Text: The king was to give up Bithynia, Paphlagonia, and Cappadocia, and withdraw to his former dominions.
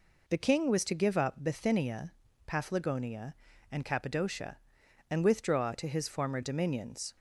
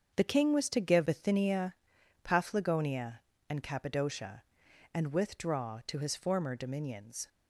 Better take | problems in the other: first | starts louder than the rest; until 1.1 s; 7 dB // skips "up"; at 1.0 s

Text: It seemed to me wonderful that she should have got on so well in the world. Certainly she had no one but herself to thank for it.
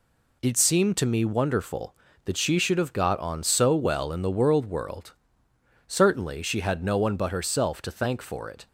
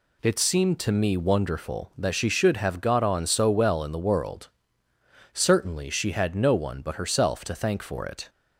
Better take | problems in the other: second | says "world" twice; at 4.6 s

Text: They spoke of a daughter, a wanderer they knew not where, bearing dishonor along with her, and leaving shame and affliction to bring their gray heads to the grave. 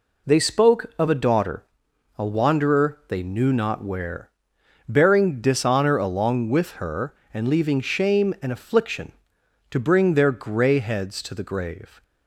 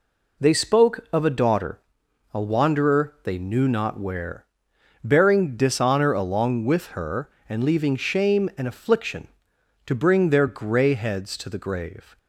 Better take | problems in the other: neither | none

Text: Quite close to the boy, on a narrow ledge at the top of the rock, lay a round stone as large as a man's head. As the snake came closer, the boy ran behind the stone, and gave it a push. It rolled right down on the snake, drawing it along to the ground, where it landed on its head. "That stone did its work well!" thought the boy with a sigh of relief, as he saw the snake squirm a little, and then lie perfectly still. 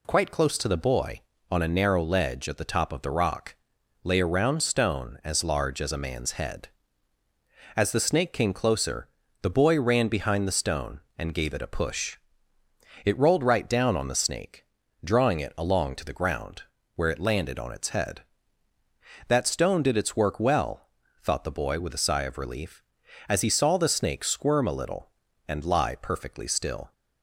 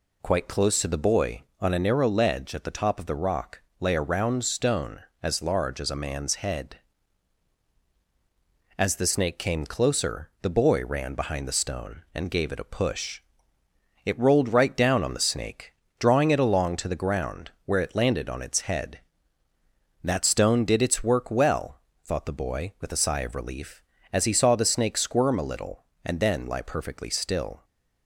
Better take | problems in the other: second | skips "then"; at 25.6 s

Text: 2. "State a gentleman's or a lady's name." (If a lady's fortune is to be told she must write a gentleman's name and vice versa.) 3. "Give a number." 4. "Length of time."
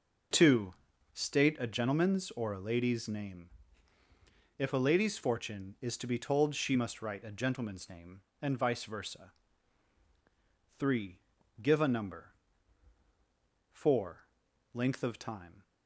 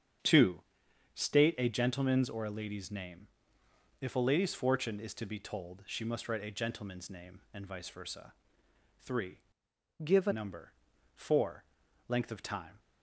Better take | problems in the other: first | starts louder than the rest; strong; until 1.8 s; 7.5 dB // changes voice from "Give" to "a"; from 10.0 to 10.3 s; 0.3 s long

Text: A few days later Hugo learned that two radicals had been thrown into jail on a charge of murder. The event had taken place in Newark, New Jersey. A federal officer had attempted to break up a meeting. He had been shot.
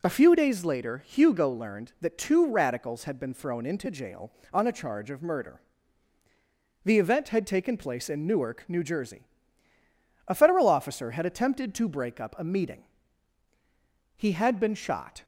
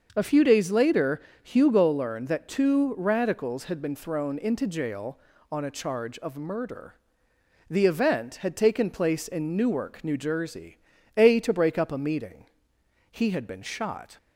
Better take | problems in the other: first | starts louder than the rest; until 1.1 s; 6.5 dB // pauses between "later" and "Hugo"; slight; at 1.2 s; 0.22 s long // skips "federal officer had attempted"; at 11.3 s

